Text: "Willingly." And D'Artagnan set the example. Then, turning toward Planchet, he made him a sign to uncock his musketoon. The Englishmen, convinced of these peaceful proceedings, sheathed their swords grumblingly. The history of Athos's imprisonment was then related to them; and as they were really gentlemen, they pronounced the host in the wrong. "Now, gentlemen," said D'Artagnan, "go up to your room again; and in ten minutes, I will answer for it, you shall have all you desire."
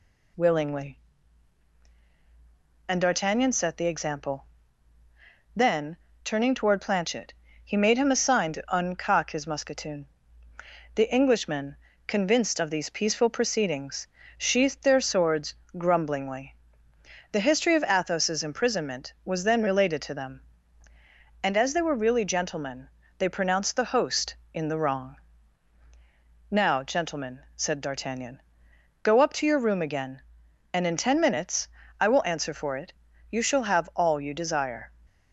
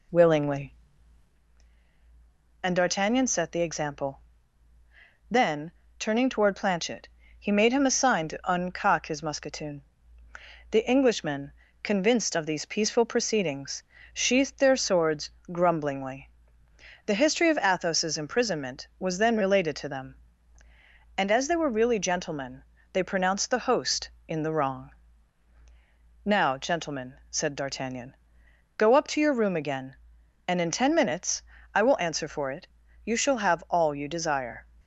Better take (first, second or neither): first